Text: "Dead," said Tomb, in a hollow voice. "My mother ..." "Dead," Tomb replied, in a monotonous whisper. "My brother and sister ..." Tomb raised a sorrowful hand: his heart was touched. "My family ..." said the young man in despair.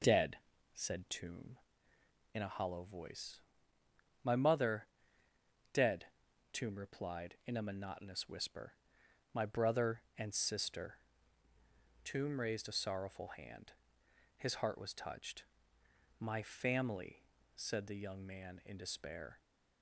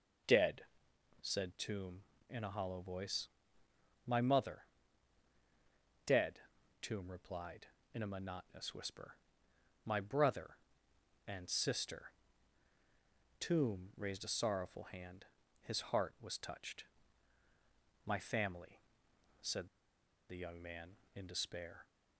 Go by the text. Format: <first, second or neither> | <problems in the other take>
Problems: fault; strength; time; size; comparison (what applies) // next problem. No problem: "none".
first | pauses between "said" and "the"; noticeable; at 19.6 s; 0.61 s long